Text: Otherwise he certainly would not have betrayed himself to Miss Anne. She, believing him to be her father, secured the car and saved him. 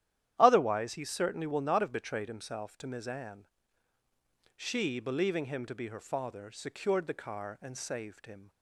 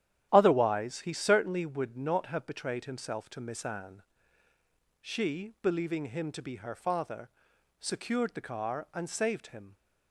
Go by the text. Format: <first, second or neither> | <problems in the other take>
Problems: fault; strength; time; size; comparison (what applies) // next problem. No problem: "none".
second | starts louder than the rest; strong; until 1.3 s; 11.5 dB; strong in the second // says "will" for "would"; at 1.4 s